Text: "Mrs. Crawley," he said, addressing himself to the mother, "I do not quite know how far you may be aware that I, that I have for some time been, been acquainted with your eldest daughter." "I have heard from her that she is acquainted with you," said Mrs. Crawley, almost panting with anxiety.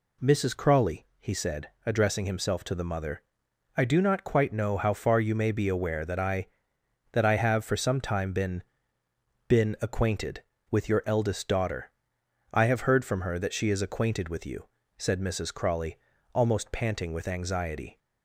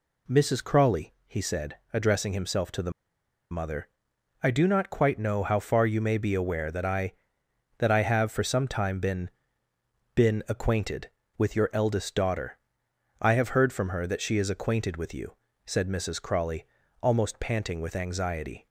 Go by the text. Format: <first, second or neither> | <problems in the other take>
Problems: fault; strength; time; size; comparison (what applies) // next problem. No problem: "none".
first | pauses between "the" and "mother"; noticeable; at 2.9 s; 0.59 s long